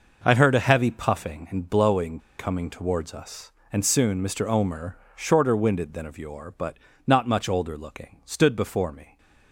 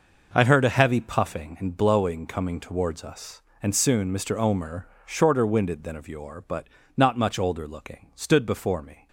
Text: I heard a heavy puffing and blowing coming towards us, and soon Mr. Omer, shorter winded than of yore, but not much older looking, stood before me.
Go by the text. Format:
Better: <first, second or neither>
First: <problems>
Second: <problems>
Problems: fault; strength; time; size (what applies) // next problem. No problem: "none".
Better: second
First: pauses between "blowing" and "coming"; slight; at 2.2 s; 0.17 s long // pauses between "but" and "not"; slight; at 6.7 s; 0.26 s long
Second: pauses between "but" and "not"; slight; at 6.6 s; 0.26 s long